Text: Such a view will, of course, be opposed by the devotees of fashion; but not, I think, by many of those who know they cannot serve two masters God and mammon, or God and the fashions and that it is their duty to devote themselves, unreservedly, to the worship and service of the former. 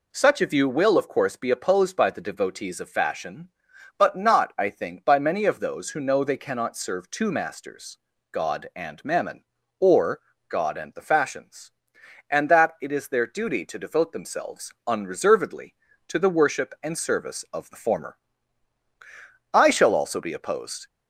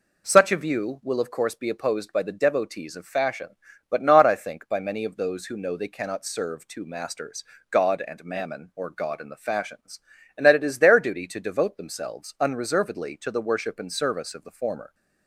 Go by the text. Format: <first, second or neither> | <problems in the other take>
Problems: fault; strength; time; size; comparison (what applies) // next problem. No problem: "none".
second | pauses between "masters" and "God"; slight; at 7.9 s; 0.34 s long; slight in the second // pauses between "or" and "God"; slight; at 10.2 s; 0.28 s long // goes on to say "I shall also be opposed"; from 19.5 s on; 1.3 s long